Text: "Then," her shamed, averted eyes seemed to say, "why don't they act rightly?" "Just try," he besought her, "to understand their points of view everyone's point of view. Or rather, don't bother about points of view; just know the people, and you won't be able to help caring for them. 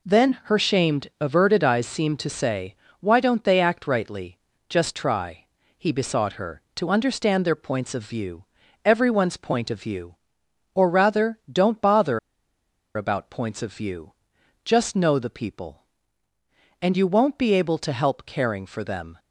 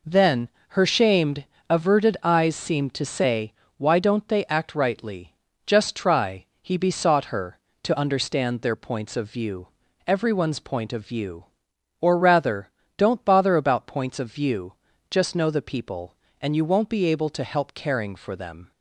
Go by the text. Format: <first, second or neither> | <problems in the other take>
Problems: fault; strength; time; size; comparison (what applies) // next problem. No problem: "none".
second | pauses between "view" and "everyone's"; at 8.4 s; 0.40 s long; also in the second // pauses between "bother" and "about"; noticeable; at 12.1 s; 0.76 s long